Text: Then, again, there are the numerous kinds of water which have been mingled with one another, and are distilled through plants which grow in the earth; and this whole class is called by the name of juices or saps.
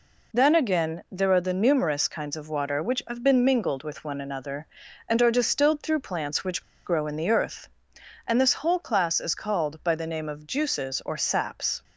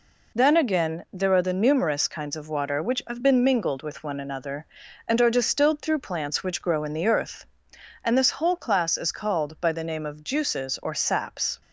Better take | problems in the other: second | pauses between "which" and "grow"; slight; at 6.6 s; 0.24 s long

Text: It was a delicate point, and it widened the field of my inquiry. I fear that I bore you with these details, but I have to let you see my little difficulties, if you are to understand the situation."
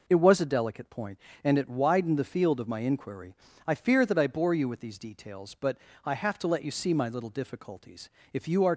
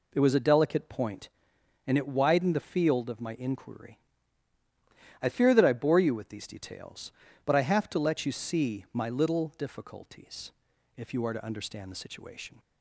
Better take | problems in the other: second | pauses between "but" and "I"; slight; at 5.7 s; 0.28 s long // stops before "to understand the situation"; at 8.7 s

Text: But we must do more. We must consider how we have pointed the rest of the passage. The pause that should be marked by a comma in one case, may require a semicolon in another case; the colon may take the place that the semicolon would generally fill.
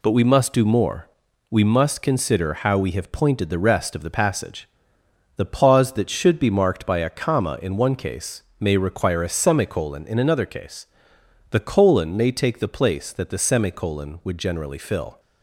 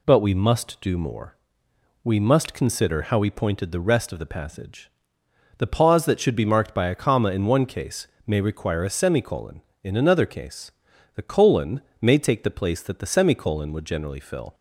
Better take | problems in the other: first | skips "have"; at 3.3 s // pauses between "colon" and "may"; slight; at 11.8 s; 0.20 s long

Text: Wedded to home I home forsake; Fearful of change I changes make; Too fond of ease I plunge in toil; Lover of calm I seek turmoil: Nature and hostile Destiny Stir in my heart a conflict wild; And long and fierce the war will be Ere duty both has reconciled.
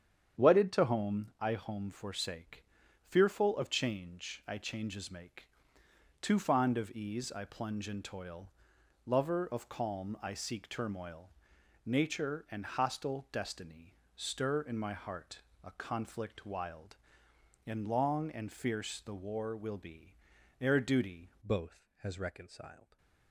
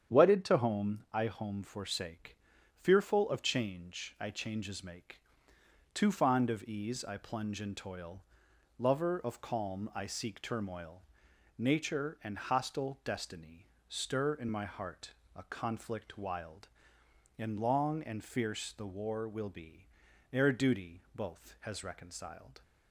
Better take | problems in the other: second | starts louder than the rest; strong; until 1.5 s; 8.5 dB; strong in the second // pauses between "Destiny" and "Stir"; slight; at 13.9 s; 0.20 s long; slight in the second // pauses between "heart" and "a"; slight; at 15.3 s; 0.24 s long; slight in the second // pauses between "be" and "Ere"; noticeable; at 20.1 s; 0.46 s long; noticeable in the second // changes voice at "both"; from 21.4 s on; 1.5 s long // stays silent after the last word; slight; from 22.8 s on; 0.5 s long

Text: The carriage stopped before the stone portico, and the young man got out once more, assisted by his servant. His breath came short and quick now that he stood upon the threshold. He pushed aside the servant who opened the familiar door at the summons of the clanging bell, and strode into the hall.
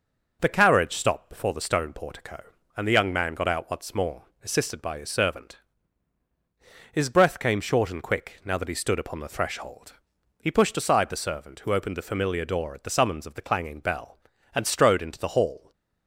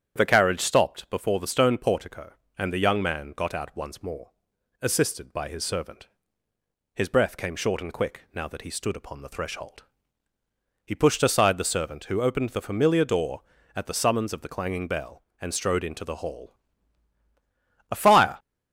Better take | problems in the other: first | starts louder than the rest; strong; until 1.2 s; 9 dB // goes on to say "A fire"; slight; from 17.9 s on; 0.48 s long

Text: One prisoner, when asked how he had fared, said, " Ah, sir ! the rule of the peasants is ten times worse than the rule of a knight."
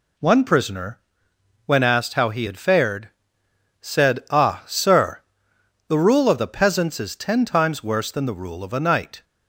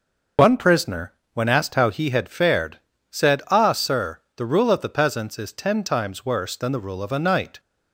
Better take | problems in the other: first | loses the start of "One"; at 0.3 s; 50 ms

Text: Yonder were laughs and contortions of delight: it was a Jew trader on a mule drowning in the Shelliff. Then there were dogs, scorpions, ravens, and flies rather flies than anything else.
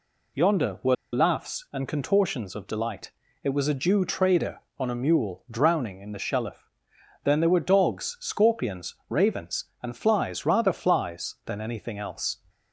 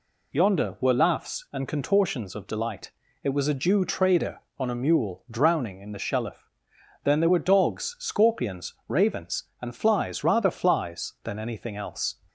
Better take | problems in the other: second | pauses between "were" and "laughs"; slight; at 0.9 s; 0.17 s long

